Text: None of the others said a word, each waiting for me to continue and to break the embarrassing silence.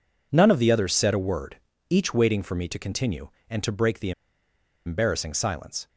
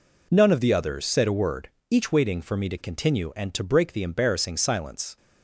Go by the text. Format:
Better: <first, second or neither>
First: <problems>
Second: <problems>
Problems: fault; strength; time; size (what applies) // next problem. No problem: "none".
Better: second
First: pauses between "the" and "embarrassing"; noticeable; at 4.1 s; 0.74 s long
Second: none